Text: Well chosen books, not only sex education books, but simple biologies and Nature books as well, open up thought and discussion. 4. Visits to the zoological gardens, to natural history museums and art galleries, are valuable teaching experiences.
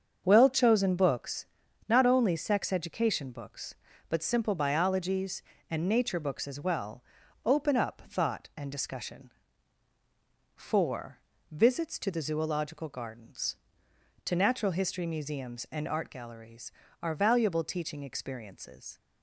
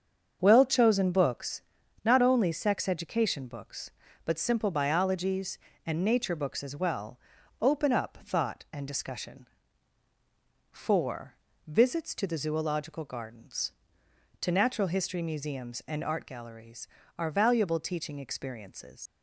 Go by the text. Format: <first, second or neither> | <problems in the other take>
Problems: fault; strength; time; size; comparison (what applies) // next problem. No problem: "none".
first | starts louder than the rest; until 1.4 s; 7 dB; also in the first // leaves "experiences" unfinished; at 19.0 s; 70 ms